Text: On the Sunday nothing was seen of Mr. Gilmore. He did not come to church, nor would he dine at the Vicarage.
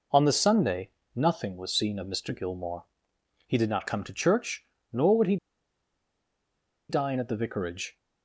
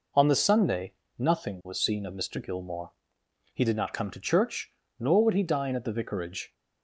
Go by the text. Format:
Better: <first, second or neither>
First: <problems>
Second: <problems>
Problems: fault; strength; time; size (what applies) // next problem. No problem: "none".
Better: second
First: pauses between "Sunday" and "nothing"; slight; at 0.8 s; 0.26 s long // pauses between "he" and "dine"; strong; at 5.3 s; 1.5 s long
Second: pauses between "Sunday" and "nothing"; slight; at 0.9 s; 0.26 s long